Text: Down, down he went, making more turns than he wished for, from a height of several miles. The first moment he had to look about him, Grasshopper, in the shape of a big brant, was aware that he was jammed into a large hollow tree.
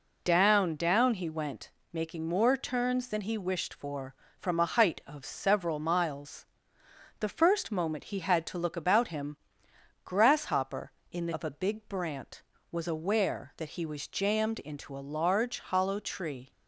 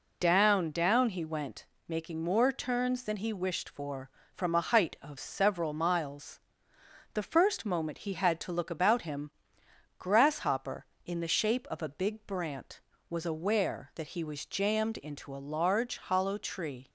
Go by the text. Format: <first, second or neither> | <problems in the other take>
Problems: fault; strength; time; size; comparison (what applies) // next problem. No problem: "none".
second | skips "shape"; at 11.3 s